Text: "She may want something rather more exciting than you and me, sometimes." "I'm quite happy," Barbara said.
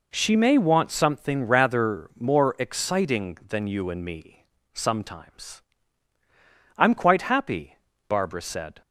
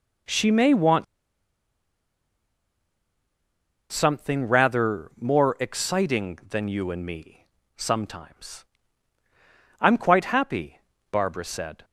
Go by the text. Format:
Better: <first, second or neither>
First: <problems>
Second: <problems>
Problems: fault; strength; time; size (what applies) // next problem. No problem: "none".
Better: first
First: none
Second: pauses between "want" and "something"; strong; at 1.0 s; 2.8 s long